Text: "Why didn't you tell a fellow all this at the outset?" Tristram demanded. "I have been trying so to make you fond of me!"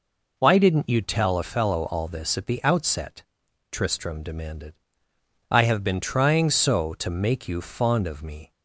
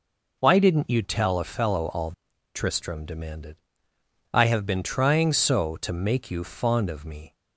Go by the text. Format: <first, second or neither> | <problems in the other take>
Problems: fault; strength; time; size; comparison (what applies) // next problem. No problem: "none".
first | skips "this at the outset"; at 2.3 s